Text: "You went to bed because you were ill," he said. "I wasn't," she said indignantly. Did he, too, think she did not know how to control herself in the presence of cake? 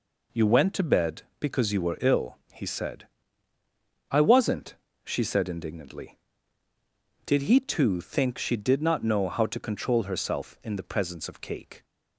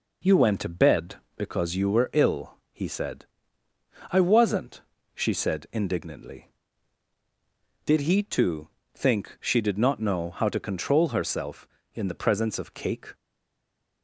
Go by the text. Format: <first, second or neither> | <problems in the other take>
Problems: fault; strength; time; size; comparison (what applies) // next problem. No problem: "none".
first | stays silent after the last word; slight; from 13.1 s on; 0.9 s long